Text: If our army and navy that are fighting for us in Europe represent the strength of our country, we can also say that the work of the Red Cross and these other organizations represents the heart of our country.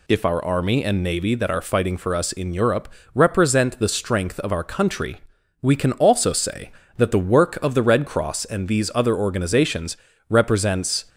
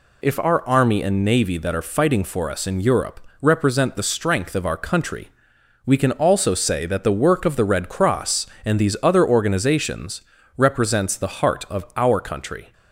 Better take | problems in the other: second | pauses between "Europe" and "represent"; slight; at 2.8 s; 0.26 s long; slight in the second // pauses between "organizations" and "represents"; slight; at 9.9 s; 0.32 s long; slight in the second // stops before "the heart of our country"; at 11.0 s

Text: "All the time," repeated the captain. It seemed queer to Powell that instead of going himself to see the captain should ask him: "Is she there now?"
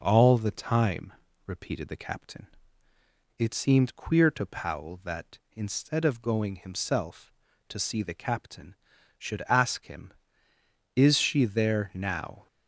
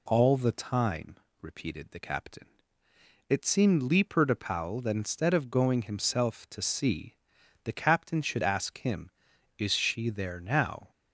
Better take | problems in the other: first | says "leaper" for "queer"; at 3.8 s // pauses between "see" and "the"; noticeable; at 7.1 s; 0.48 s long

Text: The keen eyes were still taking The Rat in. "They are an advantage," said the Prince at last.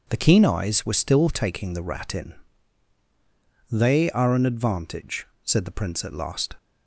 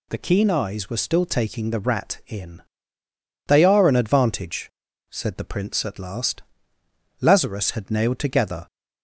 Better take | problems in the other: first | goes on to say "Lazarus had nailed together"; from 7.2 s on; 1.4 s long

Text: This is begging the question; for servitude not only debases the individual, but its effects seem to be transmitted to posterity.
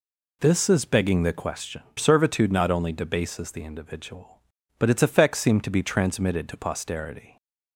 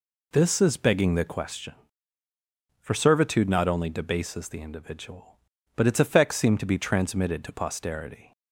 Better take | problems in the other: second | skips "for"; at 1.8 s

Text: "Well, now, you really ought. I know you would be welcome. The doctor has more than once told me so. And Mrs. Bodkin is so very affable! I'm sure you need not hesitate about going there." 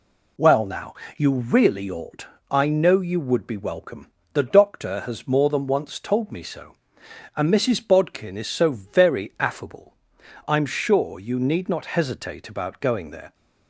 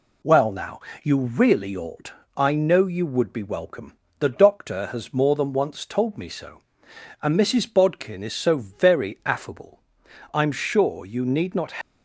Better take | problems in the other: first | stops before "hesitate about going there"; at 11.8 s

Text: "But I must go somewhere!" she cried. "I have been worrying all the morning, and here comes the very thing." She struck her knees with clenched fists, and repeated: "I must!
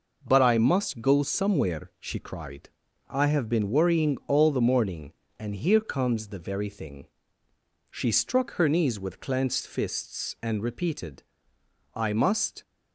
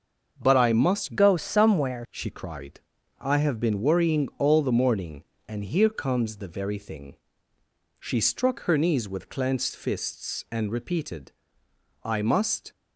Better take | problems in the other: first | starts louder than the rest; until 1.4 s; 6.5 dB // changes voice from "go" to "somewhere"; from 1.1 to 2.0 s; 0.9 s long

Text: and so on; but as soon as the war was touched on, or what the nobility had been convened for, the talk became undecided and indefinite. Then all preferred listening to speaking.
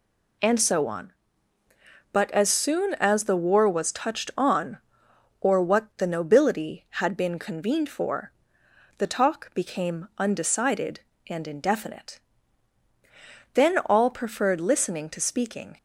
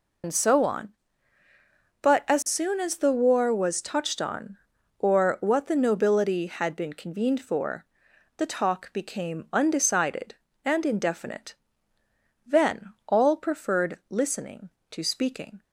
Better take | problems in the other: first | loses the start of "and"; at 0.2 s; 90 ms

